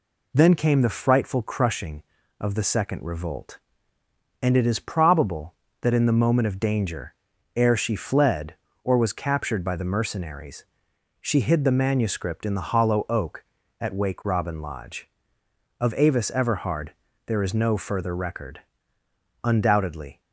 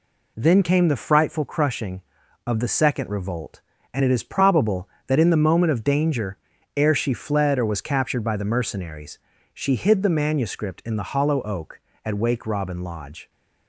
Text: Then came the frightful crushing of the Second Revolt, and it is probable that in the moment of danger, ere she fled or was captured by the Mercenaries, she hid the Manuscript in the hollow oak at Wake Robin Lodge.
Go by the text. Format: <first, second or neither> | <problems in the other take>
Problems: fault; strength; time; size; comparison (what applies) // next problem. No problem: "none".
second | goes on to say "Of Avis Everhard there is no further record Undoubtedly"; strong; from 15.8 s on; 4.4 s long